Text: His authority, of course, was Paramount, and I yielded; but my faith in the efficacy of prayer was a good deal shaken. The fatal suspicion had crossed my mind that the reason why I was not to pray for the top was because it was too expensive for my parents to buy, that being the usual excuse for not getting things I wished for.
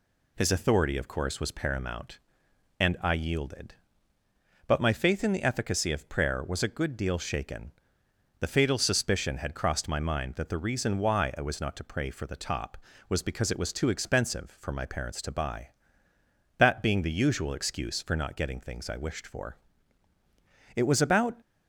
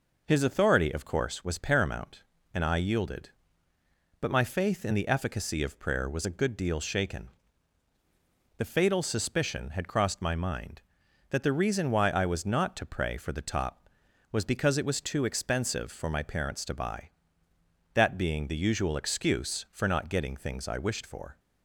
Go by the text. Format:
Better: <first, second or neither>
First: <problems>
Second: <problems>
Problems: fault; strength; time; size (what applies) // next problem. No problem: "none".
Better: second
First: goes on to say "It was about"; noticeable; from 20.7 s on; 0.62 s long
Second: none